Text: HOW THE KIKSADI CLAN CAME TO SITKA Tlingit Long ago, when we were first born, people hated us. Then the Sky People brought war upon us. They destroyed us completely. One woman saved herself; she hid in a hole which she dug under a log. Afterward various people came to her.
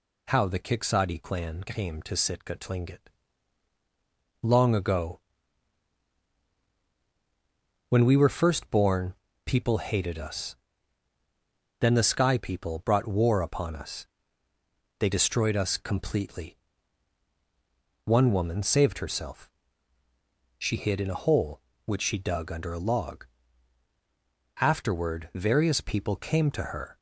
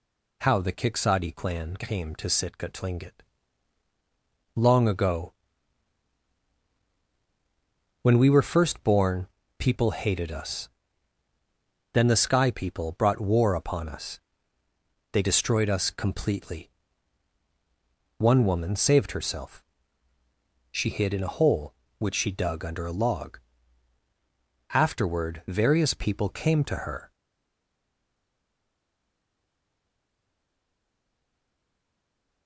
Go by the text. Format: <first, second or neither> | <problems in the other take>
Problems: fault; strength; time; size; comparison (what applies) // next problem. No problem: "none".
first | pauses between "Tlingit" and "Long"; strong; at 3.2 s; 1.3 s long; strong in the first // stays silent after the last word; strong; from 27.1 s on; 5.3 s long